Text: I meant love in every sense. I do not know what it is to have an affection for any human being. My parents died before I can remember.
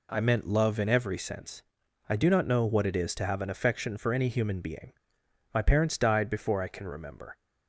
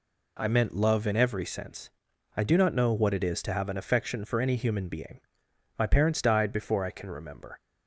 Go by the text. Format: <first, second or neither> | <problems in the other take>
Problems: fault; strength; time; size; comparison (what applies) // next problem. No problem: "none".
neither | none